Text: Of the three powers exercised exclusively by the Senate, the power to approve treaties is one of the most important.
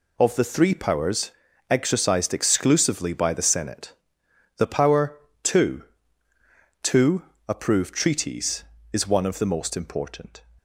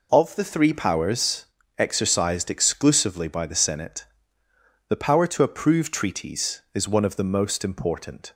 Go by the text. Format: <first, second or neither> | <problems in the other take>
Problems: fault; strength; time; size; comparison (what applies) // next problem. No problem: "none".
second | pauses between "powers" and "exercised"; at 1.3 s; 0.38 s long; slight in the second // says "to" twice; at 6.8 s